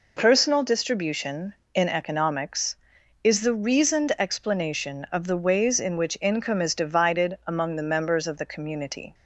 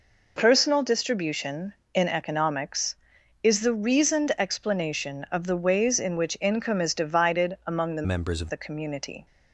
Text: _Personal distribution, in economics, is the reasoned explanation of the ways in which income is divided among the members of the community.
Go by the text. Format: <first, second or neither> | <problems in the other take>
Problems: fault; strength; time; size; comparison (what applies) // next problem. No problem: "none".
first | changes voice from "members" to "of"; from 8.0 to 8.5 s; 0.5 s long